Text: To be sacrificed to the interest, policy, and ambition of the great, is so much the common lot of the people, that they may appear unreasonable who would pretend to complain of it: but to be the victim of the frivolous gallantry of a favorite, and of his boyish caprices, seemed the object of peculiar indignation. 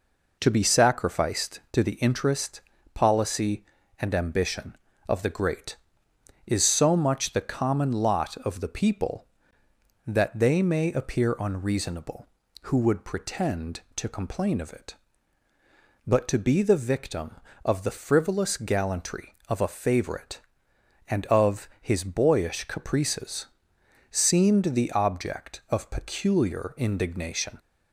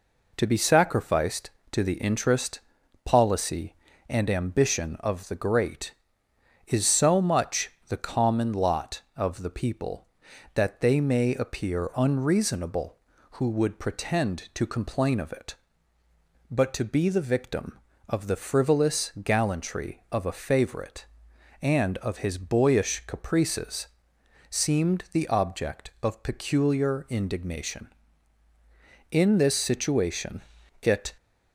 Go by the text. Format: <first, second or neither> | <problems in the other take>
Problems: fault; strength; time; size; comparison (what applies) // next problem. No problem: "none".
first | pauses between "much" and "the"; slight; at 7.7 s; 0.18 s long // goes on to say "In this situation it"; strong; from 29.1 s on; 2.0 s long